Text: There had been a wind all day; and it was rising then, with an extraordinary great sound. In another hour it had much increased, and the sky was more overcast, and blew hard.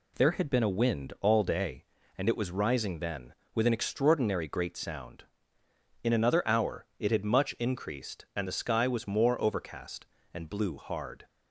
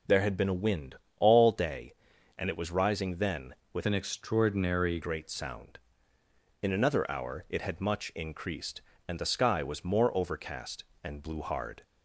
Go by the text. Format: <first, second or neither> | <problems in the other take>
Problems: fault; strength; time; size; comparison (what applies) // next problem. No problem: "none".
first | pauses between "wind" and "all"; slight; at 0.9 s; 0.24 s long // changes voice from "an" to "extraordinary"; from 3.8 to 5.0 s; 1.2 s long